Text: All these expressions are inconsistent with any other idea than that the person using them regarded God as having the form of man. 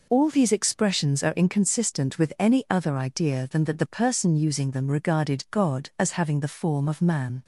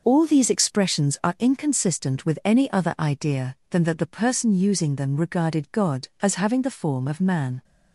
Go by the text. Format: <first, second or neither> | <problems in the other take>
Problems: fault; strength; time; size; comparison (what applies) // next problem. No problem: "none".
neither | none